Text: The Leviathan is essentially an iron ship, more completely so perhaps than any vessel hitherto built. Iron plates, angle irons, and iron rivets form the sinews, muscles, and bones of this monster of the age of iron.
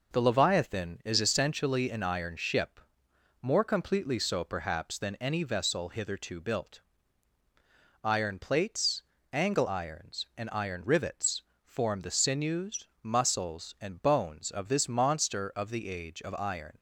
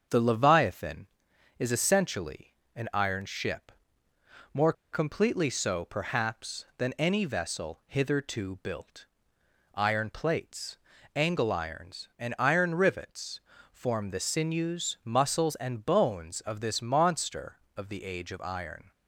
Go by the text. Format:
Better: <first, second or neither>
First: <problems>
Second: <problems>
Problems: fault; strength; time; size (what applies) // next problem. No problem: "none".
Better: first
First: pauses between "rivets" and "form"; slight; at 11.4 s; 0.22 s long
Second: starts louder than the rest; until 1.6 s; 7 dB // pauses between "essentially" and "an"; slight; at 2.5 s; 0.24 s long // pauses between "more" and "completely"; slight; at 4.7 s; 0.19 s long // pauses between "rivets" and "form"; slight; at 13.4 s; 0.32 s long